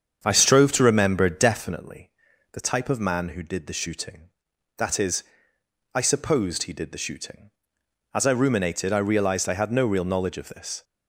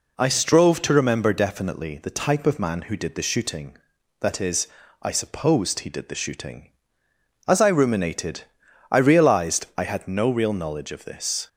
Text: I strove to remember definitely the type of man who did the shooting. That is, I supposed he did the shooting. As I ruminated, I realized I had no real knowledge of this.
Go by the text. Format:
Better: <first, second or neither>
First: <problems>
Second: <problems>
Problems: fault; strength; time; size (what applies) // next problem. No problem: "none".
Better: second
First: starts louder than the rest; strong; until 1.8 s; 7.5 dB // pauses between "definitely" and "the"; at 2.1 s; 0.40 s long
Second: none